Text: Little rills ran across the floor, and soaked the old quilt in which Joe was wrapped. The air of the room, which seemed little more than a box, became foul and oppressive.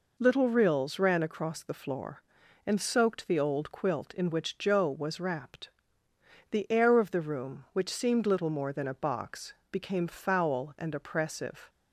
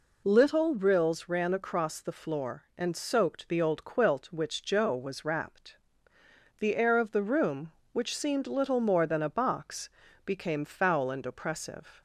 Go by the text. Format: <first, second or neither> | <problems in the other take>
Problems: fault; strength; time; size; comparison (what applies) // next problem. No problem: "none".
first | skips "in"; at 4.3 s